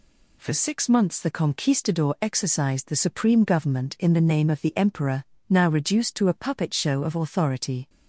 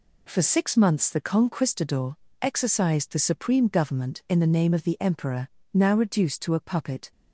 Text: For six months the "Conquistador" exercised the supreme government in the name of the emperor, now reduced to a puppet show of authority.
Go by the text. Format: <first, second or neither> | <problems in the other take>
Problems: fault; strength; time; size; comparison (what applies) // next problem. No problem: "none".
first | pauses between "Conquistador" and "exercised"; slight; at 2.1 s; 0.24 s long // stops before "show of authority"; at 7.1 s